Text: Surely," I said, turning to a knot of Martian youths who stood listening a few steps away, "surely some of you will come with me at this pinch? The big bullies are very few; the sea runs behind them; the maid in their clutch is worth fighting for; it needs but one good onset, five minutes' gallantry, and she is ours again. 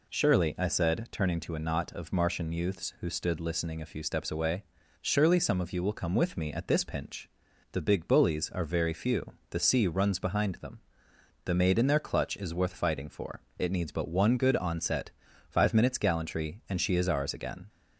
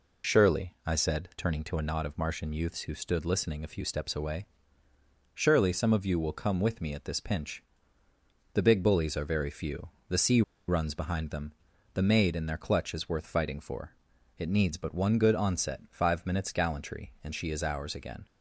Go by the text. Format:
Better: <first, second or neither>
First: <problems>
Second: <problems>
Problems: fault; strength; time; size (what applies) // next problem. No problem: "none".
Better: first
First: none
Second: pauses between "sea" and "runs"; slight; at 10.4 s; 0.26 s long